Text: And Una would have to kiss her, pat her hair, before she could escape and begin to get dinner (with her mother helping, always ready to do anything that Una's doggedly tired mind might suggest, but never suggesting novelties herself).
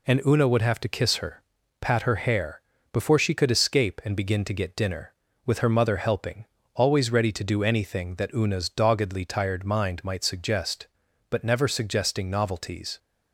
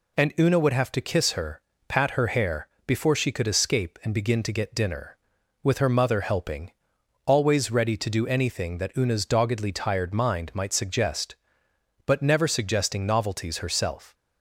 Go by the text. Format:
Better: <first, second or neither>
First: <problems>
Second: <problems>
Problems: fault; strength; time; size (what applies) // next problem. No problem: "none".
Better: second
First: stops before "herself"; at 12.9 s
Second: none